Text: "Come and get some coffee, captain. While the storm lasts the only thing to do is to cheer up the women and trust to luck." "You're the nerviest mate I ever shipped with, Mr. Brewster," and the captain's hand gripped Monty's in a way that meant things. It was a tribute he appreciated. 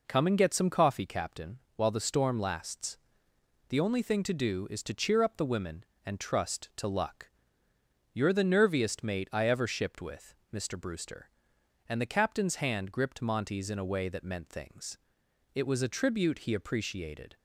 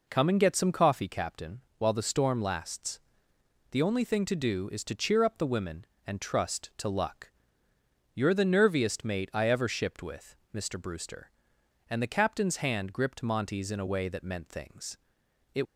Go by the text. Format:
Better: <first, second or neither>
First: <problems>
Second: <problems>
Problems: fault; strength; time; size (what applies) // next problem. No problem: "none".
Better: first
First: pauses between "lasts" and "the"; noticeable; at 2.9 s; 0.68 s long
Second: pauses between "lasts" and "the"; noticeable; at 3.0 s; 0.68 s long // stops before "was a tribute he appreciated"; at 15.6 s